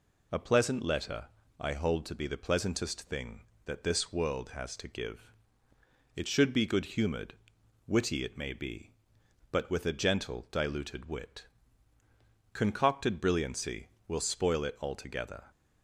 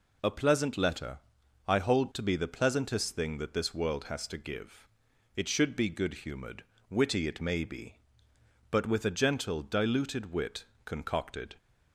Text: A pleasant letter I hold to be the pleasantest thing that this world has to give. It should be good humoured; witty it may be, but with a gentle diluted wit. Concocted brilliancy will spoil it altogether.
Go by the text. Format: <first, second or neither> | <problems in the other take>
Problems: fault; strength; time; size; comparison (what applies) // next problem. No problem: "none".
first | pauses between "letter" and "I"; noticeable; at 1.1 s; 0.46 s long; slight in the first // stops before "brilliancy will spoil it altogether"; at 11.5 s